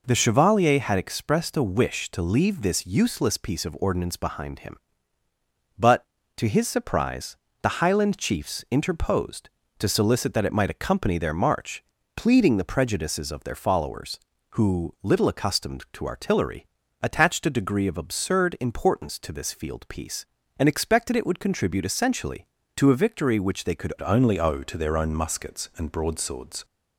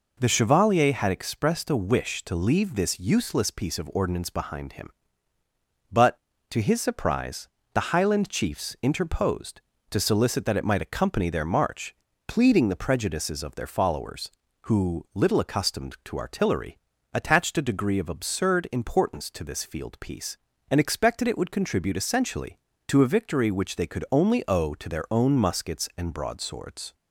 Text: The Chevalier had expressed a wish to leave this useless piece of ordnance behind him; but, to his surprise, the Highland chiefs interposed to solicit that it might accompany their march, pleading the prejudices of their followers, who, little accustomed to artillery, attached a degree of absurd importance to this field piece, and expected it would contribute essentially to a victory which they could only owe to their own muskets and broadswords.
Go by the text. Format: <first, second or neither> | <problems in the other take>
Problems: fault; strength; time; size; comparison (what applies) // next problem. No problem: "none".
second | changes voice at "only"; from 24.0 s on; 2.6 s long